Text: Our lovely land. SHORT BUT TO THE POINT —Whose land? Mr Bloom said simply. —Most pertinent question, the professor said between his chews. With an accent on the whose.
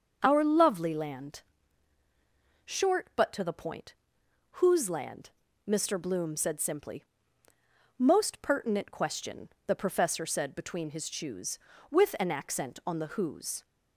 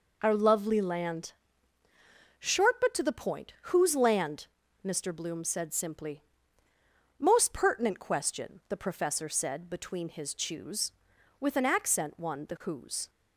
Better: first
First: none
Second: says "one" for "on"; at 12.1 s

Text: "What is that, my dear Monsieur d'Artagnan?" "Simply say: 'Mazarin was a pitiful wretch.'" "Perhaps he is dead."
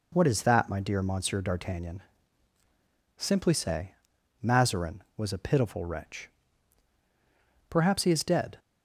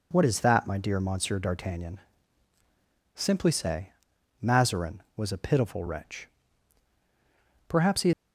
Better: first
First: none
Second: stops before "is dead"; at 8.1 s

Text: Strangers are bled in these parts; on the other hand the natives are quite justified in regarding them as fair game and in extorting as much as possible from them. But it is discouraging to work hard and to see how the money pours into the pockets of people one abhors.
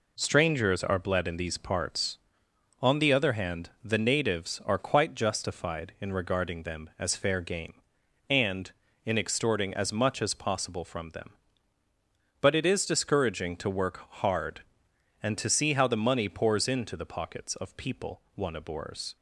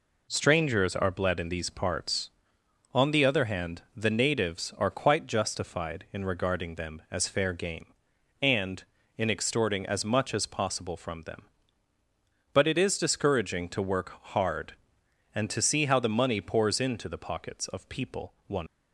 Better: first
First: pauses between "hand" and "the"; slight; at 3.6 s; 0.16 s long // pauses between "work" and "hard"; slight; at 13.9 s; 0.22 s long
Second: pauses between "hand" and "the"; slight; at 3.7 s; 0.16 s long // pauses between "work" and "hard"; slight; at 14.1 s; 0.22 s long // stops before "abhors"; at 18.6 s

